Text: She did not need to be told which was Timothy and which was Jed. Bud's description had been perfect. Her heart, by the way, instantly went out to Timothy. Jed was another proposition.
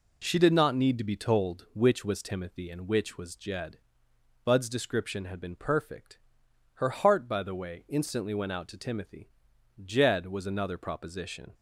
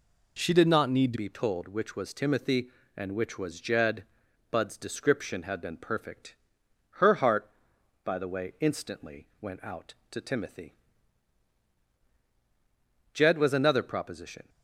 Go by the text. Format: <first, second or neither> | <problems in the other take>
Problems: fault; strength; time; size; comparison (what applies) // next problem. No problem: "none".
first | changes voice at "be"; from 1.1 s on; 13.3 s long